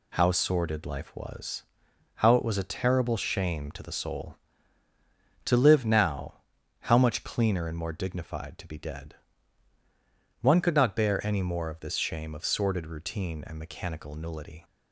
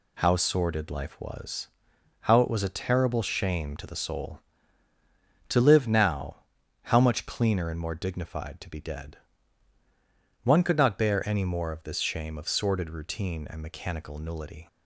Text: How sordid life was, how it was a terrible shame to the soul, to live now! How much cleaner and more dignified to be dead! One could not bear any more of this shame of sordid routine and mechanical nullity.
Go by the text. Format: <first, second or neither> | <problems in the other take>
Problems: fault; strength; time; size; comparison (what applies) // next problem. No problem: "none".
neither | none